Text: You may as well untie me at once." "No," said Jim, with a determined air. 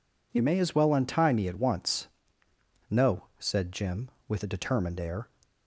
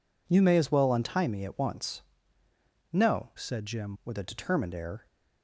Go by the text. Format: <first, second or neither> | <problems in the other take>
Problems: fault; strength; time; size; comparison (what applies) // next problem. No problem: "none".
first | changes voice from "said" to "Jim"; from 3.3 to 3.9 s; 0.6 s long